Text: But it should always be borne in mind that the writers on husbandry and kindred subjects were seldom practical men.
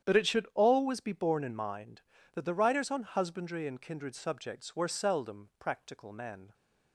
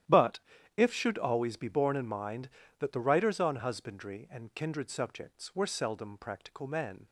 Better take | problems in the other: first | starts louder than the rest; strong; until 1.4 s; 12 dB; strong in the first // says "if" for "it"; at 0.7 s

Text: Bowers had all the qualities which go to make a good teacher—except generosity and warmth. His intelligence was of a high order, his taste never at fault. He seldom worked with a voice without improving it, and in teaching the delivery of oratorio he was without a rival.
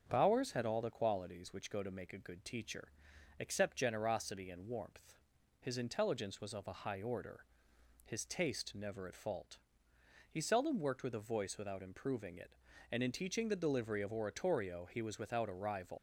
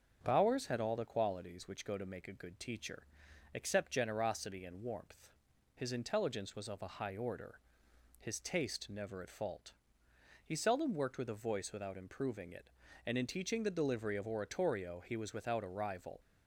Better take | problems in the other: second | starts louder than the rest; until 1.0 s; 6.5 dB; also in the second // leaves "rival" unfinished; at 15.9 s; 70 ms

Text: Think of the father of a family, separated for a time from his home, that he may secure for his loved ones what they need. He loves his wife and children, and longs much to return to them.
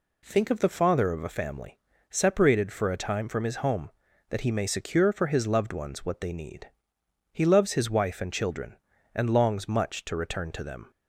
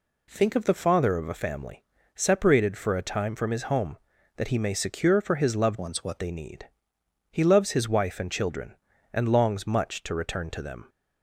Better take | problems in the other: first | changes voice from "ones" to "what"; from 5.7 to 6.1 s; 0.4 s long

